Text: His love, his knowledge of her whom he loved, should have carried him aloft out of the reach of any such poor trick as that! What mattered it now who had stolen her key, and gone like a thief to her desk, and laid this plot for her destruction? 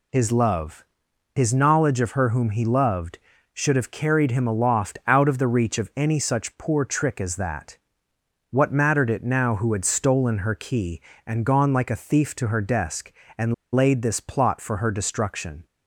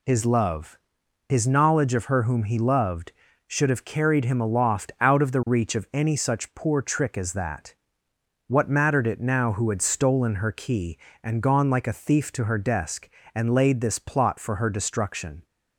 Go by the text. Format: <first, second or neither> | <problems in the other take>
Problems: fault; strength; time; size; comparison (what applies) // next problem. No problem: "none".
second | pauses between "and" and "laid"; slight; at 13.5 s; 0.21 s long